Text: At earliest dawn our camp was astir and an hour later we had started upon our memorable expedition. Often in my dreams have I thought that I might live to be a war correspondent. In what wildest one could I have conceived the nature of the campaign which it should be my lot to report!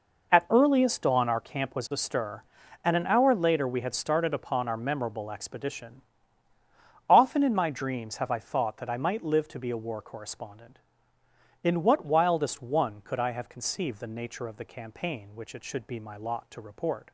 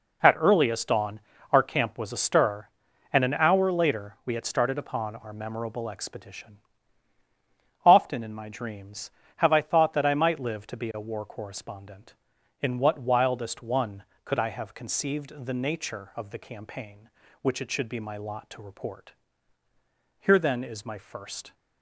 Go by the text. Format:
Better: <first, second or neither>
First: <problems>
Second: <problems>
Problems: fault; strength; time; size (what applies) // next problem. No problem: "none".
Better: first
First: none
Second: pauses between "dawn" and "our"; slight; at 1.1 s; 0.32 s long // goes on to say "Here then is my first"; from 20.1 s on; 1.3 s long